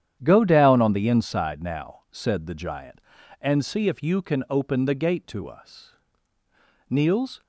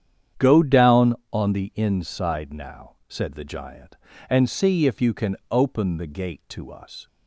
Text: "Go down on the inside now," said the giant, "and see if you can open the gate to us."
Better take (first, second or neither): second